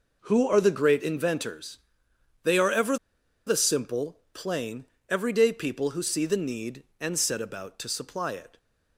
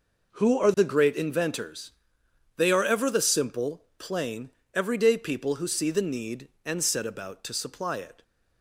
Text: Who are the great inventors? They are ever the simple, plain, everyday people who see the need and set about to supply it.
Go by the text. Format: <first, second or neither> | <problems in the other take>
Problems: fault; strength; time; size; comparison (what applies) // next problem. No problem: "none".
second | pauses between "ever" and "the"; noticeable; at 2.9 s; 0.51 s long